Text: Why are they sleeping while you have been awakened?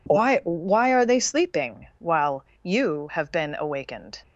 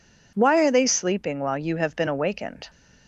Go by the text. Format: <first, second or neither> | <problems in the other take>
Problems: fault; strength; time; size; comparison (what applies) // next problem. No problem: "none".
second | says "Why" twice; at 0.4 s // pauses between "while" and "you"; slight; at 2.4 s; 0.18 s long